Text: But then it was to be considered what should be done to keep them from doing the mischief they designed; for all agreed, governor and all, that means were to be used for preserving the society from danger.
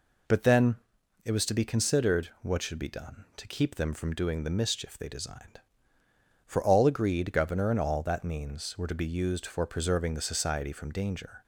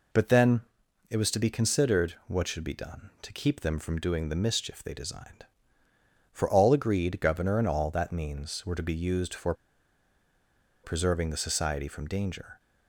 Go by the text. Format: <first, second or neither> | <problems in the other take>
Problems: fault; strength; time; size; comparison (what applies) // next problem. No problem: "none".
first | pauses between "then" and "it"; noticeable; at 0.6 s; 0.48 s long; noticeable in the first // pauses between "for" and "preserving"; strong; at 9.5 s; 1.3 s long